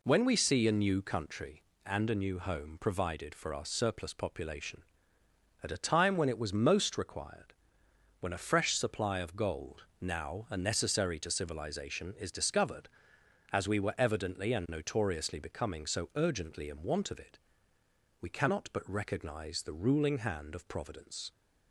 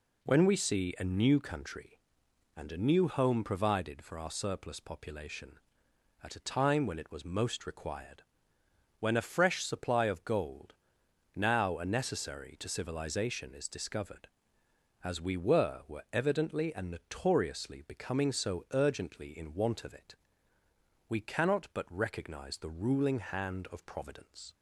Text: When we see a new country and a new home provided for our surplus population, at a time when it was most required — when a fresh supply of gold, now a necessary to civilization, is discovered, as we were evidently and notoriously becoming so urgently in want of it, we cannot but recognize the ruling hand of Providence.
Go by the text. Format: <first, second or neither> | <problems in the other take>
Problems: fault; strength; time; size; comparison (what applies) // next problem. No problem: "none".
first | says "were" twice; at 15.8 s